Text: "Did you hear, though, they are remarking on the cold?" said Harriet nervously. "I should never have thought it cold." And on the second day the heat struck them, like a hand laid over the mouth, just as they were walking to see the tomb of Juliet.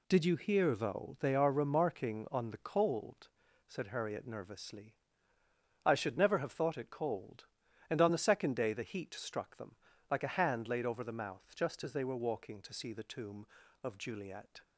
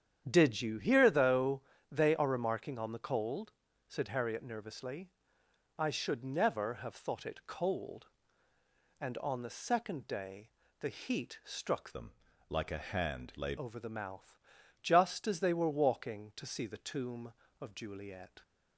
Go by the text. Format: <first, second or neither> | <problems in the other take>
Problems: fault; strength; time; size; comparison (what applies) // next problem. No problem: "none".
first | starts louder than the rest; strong; until 1.2 s; 9 dB // pauses between "day" and "the"; slight; at 10.4 s; 0.32 s long // changes voice from "them" to "laid"; from 11.9 to 13.5 s; 1.6 s long